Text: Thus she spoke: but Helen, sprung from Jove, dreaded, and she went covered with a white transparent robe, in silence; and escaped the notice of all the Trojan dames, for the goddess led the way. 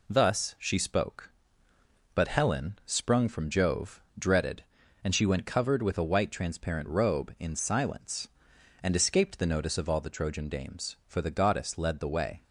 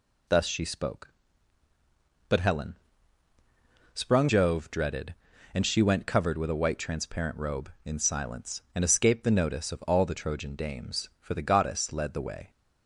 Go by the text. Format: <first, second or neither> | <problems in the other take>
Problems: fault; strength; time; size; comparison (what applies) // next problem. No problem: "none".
first | skips "from"; at 4.2 s